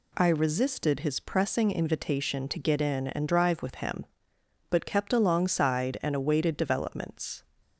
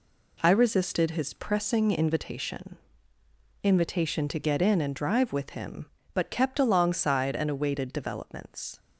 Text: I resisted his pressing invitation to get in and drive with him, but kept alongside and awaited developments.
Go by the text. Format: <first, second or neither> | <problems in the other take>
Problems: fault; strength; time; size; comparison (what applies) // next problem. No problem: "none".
first | says "invitation" twice; at 3.6 s